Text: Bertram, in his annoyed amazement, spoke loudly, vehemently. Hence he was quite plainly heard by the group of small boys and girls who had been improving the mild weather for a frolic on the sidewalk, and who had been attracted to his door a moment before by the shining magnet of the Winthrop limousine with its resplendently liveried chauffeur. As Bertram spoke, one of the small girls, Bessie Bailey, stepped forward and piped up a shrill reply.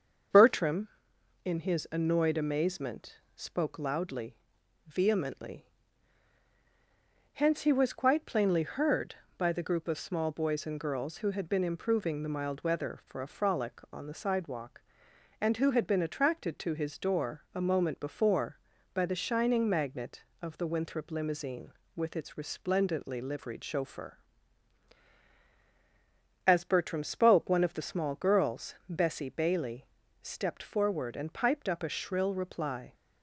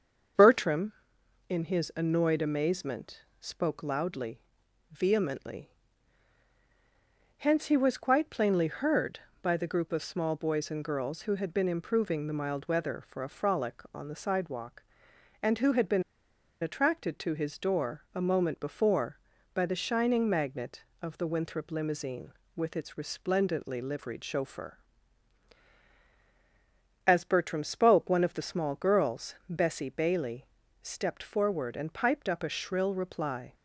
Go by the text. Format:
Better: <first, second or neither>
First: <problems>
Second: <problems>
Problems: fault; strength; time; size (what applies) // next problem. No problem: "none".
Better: first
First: starts louder than the rest; until 1.9 s; 7 dB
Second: starts louder than the rest; until 1.9 s; 7 dB // pauses between "been" and "attracted"; noticeable; at 16.0 s; 0.59 s long